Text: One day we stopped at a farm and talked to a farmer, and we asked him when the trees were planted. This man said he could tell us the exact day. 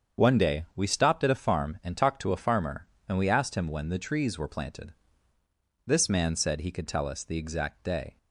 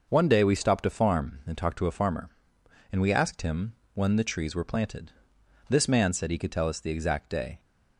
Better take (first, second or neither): first